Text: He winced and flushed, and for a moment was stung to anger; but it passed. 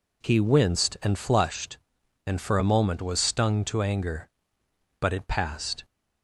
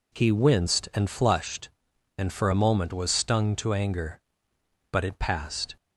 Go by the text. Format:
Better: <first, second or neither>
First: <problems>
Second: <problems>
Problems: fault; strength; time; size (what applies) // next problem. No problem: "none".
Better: neither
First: none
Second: none